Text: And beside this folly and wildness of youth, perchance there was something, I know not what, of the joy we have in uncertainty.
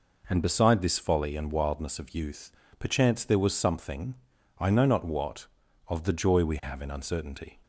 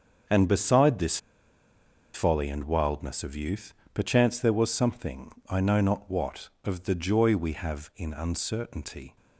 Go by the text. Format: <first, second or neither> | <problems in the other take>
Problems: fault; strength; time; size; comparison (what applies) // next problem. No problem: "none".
first | starts louder than the rest; until 2.2 s; 6.5 dB // pauses between "this" and "folly"; noticeable; at 1.1 s; 0.96 s long